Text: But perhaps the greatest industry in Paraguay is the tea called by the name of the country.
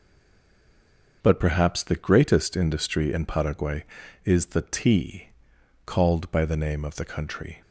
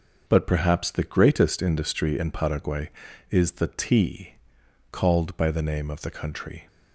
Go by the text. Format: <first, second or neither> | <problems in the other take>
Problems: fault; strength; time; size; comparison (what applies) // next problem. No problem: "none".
second | stays silent before the first word; noticeable; until 1.2 s; 1.2 s long // starts louder than the rest; until 2.2 s; 6.5 dB; also in the second // pauses between "tea" and "called"; noticeable; at 5.2 s; 0.56 s long; noticeable in the second